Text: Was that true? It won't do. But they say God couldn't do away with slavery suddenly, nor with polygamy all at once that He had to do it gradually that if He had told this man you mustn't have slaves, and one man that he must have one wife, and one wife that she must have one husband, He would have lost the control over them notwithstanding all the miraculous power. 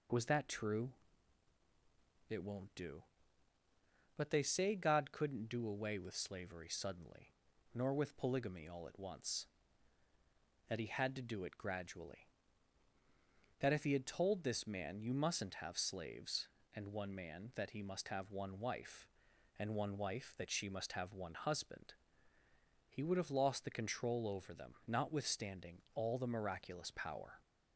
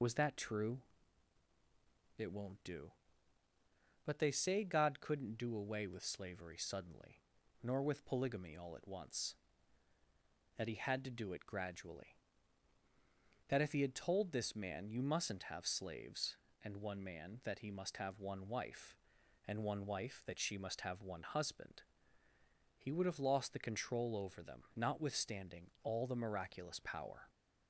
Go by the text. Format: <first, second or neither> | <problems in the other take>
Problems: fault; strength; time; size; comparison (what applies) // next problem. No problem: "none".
first | loses the start of "Was"; at 0.0 s; 25 ms // pauses between "notwithstanding" and "all"; slight; at 25.6 s; 0.16 s long; slight in the first